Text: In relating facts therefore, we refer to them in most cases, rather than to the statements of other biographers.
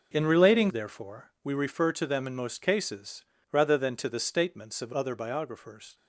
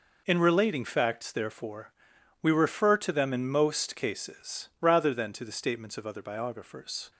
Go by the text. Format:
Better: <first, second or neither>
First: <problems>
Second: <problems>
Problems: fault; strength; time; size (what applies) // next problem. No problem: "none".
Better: second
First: skips "facts"; at 0.6 s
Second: none